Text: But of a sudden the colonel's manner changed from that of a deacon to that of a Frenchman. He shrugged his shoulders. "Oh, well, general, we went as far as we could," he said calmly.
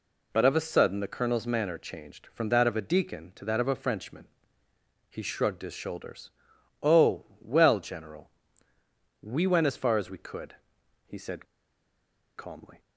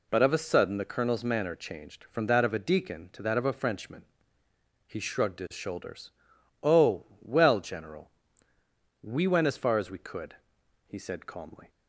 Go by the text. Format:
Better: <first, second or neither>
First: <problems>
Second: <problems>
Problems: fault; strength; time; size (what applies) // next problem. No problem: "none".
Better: second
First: pauses between "said" and "calmly"; noticeable; at 11.4 s; 0.91 s long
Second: none